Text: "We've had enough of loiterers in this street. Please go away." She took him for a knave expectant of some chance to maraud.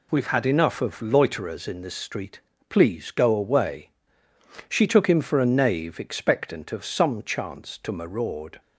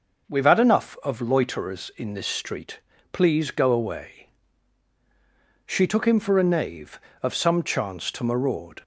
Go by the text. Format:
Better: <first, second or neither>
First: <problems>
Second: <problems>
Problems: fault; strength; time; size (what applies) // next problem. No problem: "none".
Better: first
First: none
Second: skips "expectant"; at 7.0 s